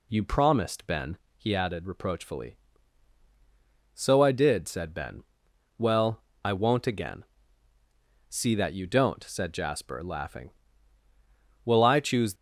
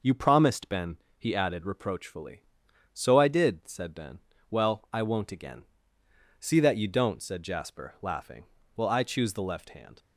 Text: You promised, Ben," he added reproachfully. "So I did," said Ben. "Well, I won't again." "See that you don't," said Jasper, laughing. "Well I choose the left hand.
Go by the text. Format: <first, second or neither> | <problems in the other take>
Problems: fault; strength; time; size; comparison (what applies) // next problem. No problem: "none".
second | stops before "the left hand"; at 12.3 s